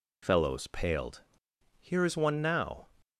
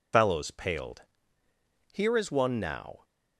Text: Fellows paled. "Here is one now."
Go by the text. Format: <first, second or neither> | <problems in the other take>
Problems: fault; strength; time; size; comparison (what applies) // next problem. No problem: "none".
first | loses the start of "Fellows"; at 0.1 s; 100 ms